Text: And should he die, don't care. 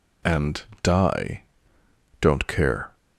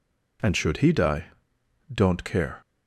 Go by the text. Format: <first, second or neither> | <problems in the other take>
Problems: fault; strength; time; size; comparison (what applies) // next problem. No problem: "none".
second | skips "should he"; at 0.7 s